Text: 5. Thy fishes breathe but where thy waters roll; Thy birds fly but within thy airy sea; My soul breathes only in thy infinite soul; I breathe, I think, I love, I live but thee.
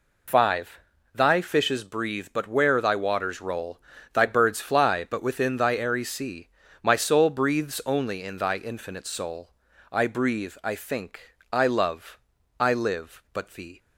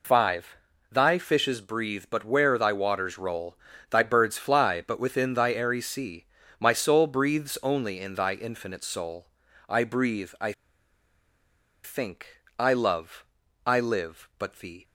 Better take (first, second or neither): first